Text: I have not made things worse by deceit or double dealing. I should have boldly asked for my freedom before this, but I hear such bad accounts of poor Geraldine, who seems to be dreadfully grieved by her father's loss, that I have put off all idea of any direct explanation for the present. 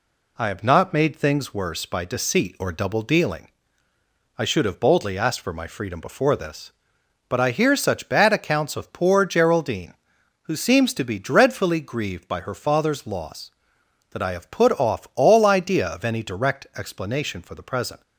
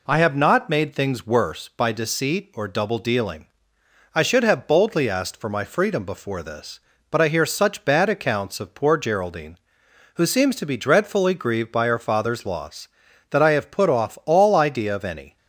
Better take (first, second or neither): first